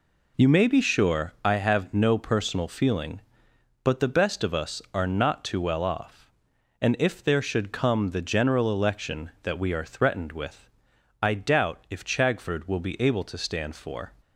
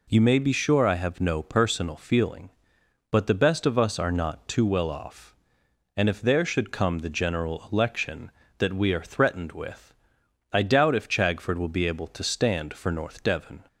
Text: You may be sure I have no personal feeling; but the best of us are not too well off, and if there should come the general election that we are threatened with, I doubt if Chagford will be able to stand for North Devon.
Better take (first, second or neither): second